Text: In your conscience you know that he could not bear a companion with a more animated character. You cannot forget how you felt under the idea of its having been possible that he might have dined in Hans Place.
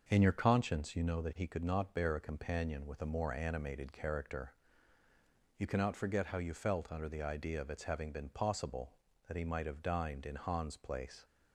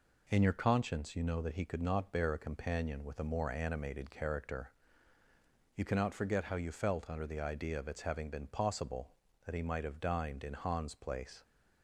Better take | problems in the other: second | starts louder than the rest; until 1.1 s; 6 dB

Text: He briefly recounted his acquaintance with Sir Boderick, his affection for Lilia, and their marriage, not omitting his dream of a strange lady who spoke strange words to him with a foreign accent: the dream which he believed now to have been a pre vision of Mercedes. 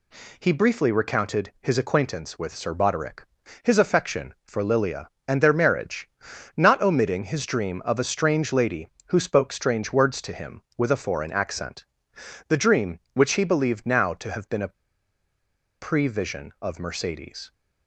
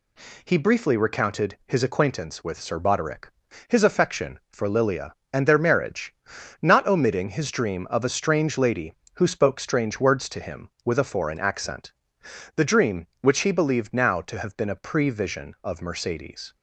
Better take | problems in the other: second | pauses between "a" and "pre"; at 14.7 s; 1.0 s long

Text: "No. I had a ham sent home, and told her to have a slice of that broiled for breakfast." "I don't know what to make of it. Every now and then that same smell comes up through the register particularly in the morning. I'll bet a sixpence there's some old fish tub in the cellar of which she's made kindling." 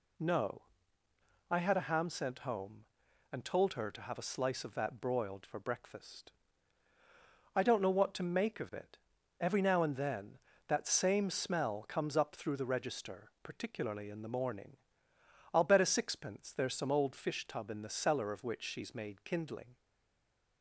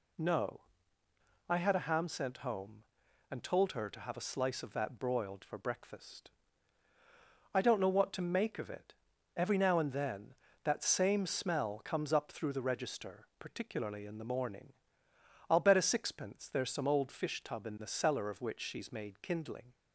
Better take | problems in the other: second | stays silent after the last word; slight; from 19.7 s on; 0.9 s long

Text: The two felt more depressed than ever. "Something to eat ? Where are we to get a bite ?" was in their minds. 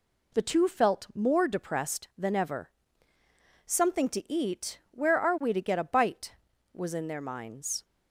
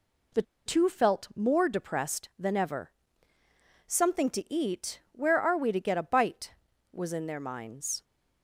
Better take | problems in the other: first | pauses between "The" and "two"; slight; at 0.4 s; 0.23 s long

